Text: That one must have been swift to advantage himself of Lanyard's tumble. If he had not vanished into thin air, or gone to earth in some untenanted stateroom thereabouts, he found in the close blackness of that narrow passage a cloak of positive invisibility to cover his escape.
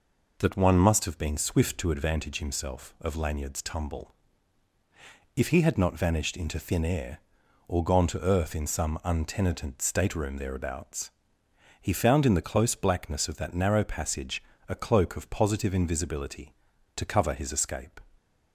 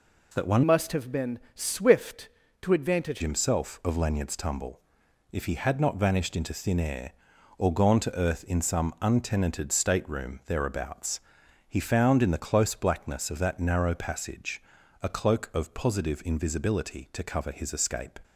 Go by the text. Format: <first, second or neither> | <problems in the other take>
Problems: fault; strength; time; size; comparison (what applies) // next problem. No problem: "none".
first | changes voice from "must" to "advantage"; from 0.6 to 3.2 s; 2.6 s long // pauses between "been" and "swift"; slight; at 1.3 s; 0.16 s long // pauses between "passage" and "a"; at 14.6 s; 0.38 s long; slight in the first